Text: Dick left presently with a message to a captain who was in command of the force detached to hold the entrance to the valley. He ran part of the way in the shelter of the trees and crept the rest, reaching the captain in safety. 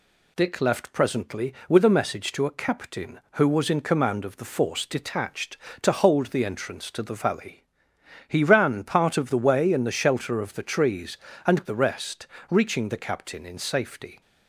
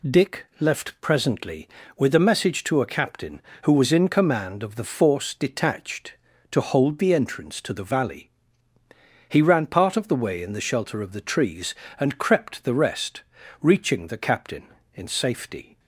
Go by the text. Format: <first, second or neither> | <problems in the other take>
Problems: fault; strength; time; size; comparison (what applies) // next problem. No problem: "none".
second | skips "crept"; at 11.6 s